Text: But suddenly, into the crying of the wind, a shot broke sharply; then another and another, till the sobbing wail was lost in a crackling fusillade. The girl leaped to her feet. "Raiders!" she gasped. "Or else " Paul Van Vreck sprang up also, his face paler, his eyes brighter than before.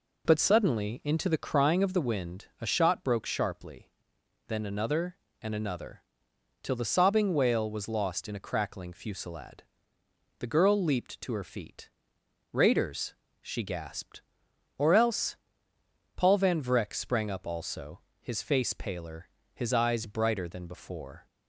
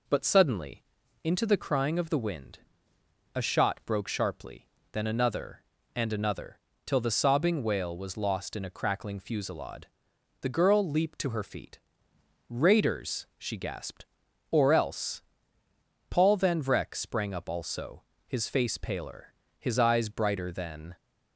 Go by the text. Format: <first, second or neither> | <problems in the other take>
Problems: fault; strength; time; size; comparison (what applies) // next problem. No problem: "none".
first | stops before "before"; at 20.9 s